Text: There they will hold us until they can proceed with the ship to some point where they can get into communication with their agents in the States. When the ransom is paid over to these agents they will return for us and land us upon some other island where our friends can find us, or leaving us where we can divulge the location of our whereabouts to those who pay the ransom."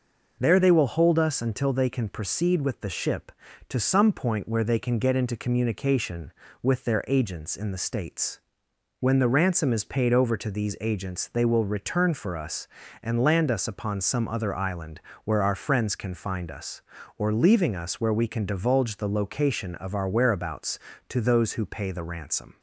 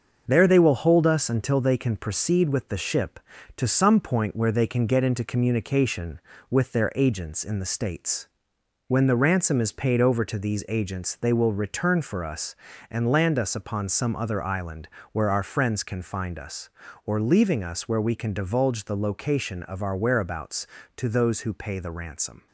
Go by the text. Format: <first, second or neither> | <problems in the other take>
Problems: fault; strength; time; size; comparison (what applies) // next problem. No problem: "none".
first | gets quieter; noticeable; throughout; 5 dB // pauses between "island" and "where"; slight; at 14.8 s; 0.24 s long; slight in the first